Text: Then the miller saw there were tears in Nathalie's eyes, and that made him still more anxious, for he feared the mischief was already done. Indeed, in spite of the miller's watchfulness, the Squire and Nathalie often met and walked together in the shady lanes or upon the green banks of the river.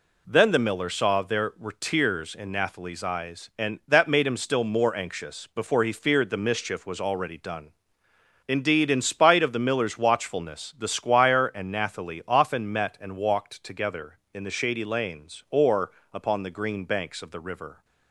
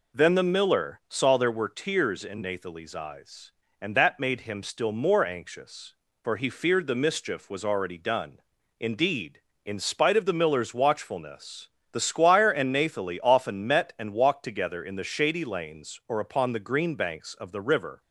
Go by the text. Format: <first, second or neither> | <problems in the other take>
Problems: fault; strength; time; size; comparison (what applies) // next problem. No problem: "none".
second | says "before" for "for"; at 5.5 s // pauses between "or" and "upon"; slight; at 15.9 s; 0.22 s long